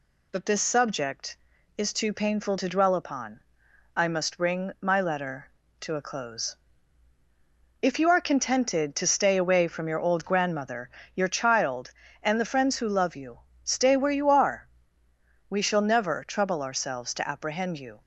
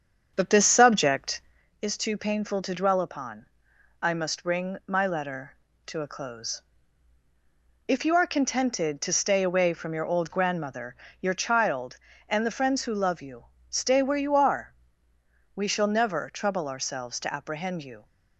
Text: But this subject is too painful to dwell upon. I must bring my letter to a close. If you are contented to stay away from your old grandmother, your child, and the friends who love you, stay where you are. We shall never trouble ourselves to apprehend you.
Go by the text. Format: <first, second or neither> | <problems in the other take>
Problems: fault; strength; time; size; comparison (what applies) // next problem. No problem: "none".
first | starts louder than the rest; strong; until 1.7 s; 7.5 dB